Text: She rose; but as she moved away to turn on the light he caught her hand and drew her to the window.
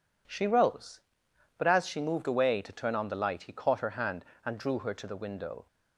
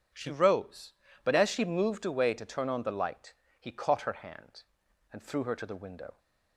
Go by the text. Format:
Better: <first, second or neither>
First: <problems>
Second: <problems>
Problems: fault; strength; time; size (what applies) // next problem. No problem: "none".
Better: first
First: none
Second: starts louder than the rest; strong; until 1.4 s; 8 dB // pauses between "light" and "he"; slight; at 3.3 s; 0.26 s long // says "threw" for "drew"; at 5.2 s